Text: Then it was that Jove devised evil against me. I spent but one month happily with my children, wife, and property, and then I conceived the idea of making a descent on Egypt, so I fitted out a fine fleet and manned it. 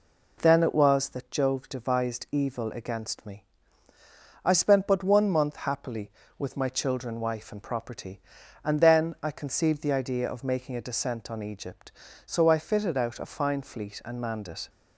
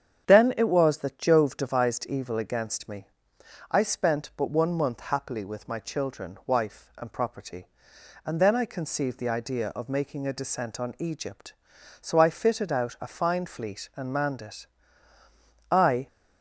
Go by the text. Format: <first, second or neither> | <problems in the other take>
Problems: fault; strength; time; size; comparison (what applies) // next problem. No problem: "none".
first | starts louder than the rest; strong; until 1.3 s; 8 dB // goes on to say "I"; slight; from 15.7 s on; 0.36 s long